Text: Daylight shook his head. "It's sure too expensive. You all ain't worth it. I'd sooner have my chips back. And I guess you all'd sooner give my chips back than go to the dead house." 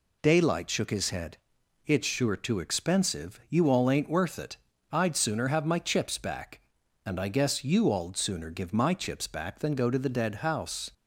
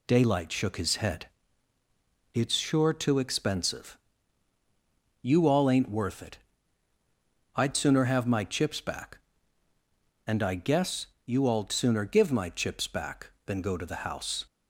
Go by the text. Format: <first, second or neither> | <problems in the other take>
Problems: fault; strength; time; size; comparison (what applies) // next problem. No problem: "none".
first | pauses between "guess" and "you"; slight; at 11.0 s; 0.20 s long // skips "dead"; at 14.0 s